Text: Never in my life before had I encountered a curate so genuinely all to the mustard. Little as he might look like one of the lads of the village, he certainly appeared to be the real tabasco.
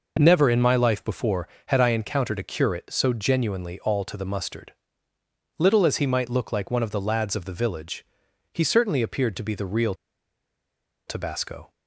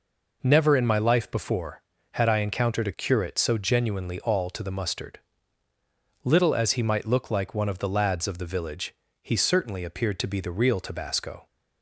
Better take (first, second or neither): second